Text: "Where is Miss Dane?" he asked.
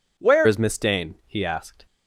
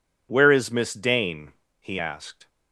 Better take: second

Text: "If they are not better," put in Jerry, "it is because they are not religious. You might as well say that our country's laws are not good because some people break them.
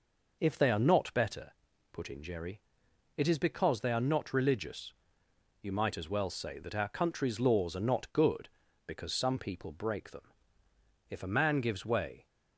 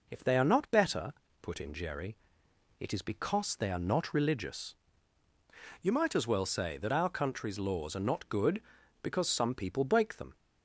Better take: second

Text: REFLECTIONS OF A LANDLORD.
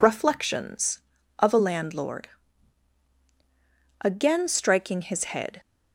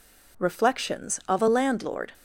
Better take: second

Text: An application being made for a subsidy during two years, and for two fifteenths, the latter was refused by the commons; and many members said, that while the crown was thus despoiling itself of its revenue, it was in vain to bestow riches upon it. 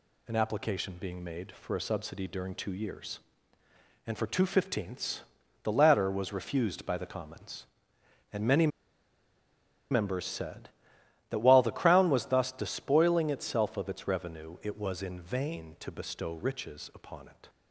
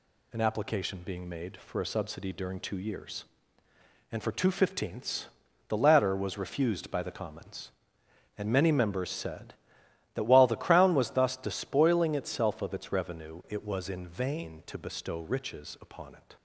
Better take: second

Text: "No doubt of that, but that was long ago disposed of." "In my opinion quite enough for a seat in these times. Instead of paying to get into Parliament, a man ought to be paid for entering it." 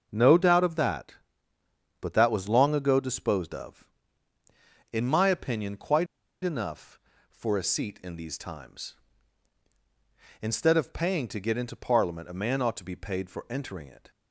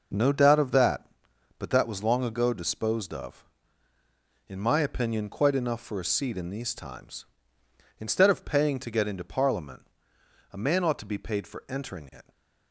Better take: second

